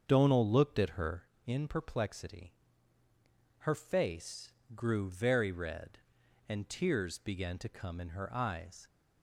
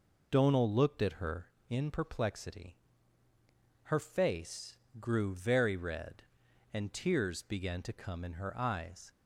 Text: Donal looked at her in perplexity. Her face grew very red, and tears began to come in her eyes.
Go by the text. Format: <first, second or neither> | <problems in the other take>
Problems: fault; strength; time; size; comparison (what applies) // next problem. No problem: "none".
second | starts louder than the rest; until 1.3 s; 7 dB // pauses between "face" and "grew"; slight; at 4.5 s; 0.24 s long; slight in the second